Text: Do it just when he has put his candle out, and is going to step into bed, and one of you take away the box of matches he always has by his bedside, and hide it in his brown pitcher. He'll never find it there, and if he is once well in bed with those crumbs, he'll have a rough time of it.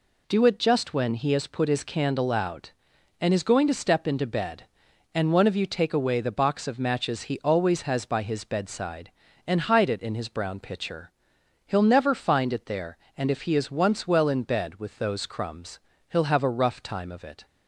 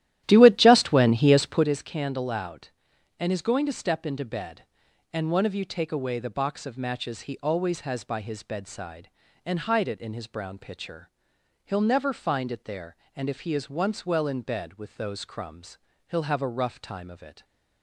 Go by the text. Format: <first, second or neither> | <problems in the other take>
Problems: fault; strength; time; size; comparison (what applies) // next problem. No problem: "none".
first | starts louder than the rest; strong; until 1.8 s; 13 dB // stays silent after the last word; slight; from 17.3 s on; 0.5 s long